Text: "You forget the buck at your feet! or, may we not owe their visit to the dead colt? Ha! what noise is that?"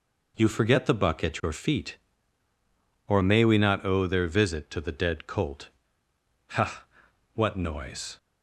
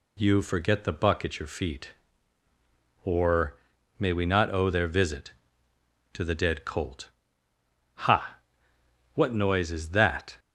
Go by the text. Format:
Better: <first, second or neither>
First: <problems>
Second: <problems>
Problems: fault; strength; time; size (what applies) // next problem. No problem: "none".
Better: second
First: stops before "is that"; at 8.1 s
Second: none